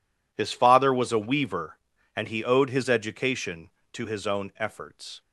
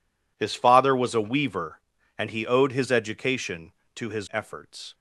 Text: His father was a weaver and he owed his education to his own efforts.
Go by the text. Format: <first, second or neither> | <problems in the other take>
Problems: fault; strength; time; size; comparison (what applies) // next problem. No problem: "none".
first | skips "own"; at 4.2 s